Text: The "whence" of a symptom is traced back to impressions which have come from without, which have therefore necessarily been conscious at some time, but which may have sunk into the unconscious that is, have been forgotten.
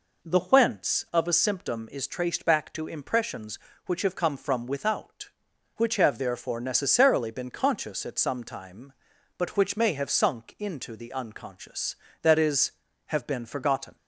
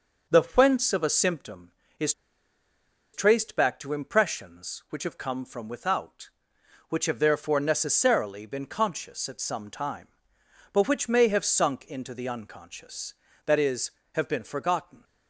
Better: first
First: none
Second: pauses between "is" and "traced"; at 2.1 s; 1.0 s long

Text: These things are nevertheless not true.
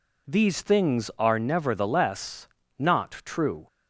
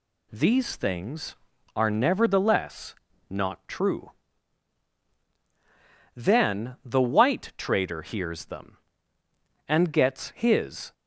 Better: first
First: pauses between "nevertheless" and "not"; slight; at 2.4 s; 0.32 s long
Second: pauses between "nevertheless" and "not"; slight; at 2.9 s; 0.36 s long // goes on to say "Then the white trader hears them and gets his"; strong; from 6.1 s on; 4.7 s long

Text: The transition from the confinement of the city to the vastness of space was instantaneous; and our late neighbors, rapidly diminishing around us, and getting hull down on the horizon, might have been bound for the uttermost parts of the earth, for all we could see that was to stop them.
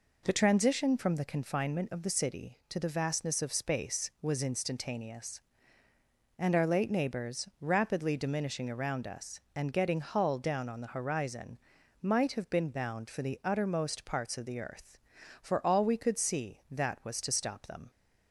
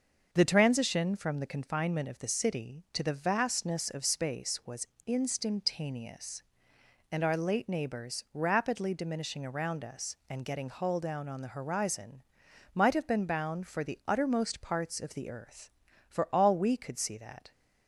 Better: first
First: none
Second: starts louder than the rest; noticeable; until 1.3 s; 6 dB // pauses between "was" and "instantaneous"; slight; at 4.8 s; 0.18 s long // stops before "was to stop them"; at 17.5 s

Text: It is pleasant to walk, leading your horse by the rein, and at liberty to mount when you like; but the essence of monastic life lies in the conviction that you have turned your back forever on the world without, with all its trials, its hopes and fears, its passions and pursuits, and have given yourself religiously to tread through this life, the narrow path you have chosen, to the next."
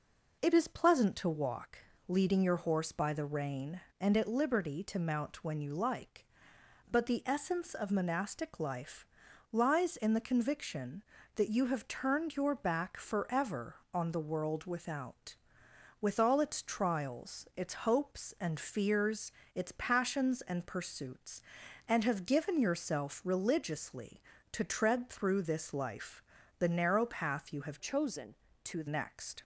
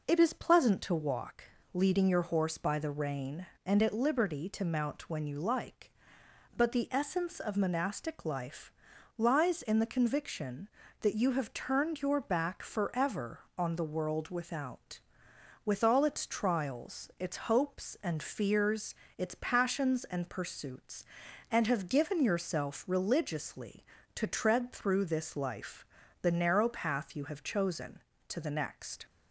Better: second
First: pauses between "life" and "lies"; noticeable; at 9.0 s; 0.46 s long // changes voice from "chosen" to "the"; from 27.7 to 28.8 s; 1.1 s long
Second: pauses between "life" and "lies"; noticeable; at 8.6 s; 0.46 s long

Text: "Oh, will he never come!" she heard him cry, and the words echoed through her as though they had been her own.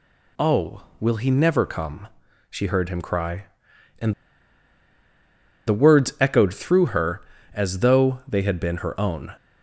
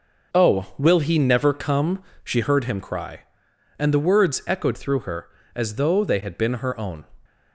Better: second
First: pauses between "and" and "the"; strong; at 4.1 s; 1.5 s long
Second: none

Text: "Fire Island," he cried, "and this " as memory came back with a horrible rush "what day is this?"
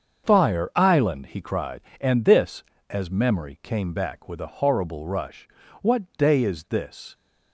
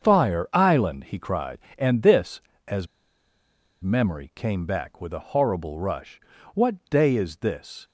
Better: first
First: starts louder than the rest; until 1.3 s; 7 dB // pauses between "rush" and "what"; slight; at 5.4 s; 0.36 s long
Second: starts louder than the rest; until 1.0 s; 7 dB // pauses between "as" and "memory"; noticeable; at 2.8 s; 0.95 s long // pauses between "rush" and "what"; slight; at 6.1 s; 0.36 s long

